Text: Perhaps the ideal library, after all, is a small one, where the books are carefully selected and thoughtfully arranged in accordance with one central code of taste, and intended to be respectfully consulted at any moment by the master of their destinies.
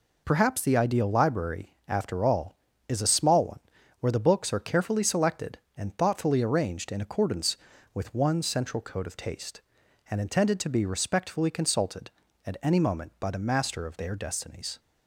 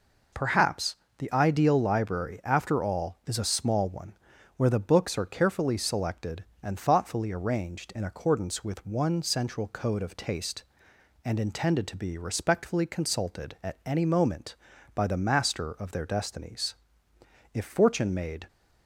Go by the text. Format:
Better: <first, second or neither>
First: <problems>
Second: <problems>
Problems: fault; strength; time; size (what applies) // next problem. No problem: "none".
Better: first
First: none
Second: pauses between "Perhaps" and "the"; slight; at 0.9 s; 0.22 s long // goes on to say "If fortune made"; noticeable; from 17.5 s on; 0.94 s long